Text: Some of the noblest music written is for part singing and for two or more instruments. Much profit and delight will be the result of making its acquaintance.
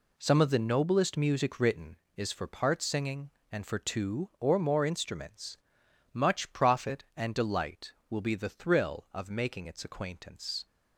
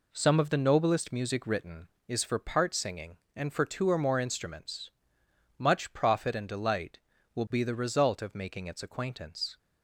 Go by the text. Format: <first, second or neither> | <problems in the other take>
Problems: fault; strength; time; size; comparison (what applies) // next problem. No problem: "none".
second | says "thrill" for "result"; at 8.4 s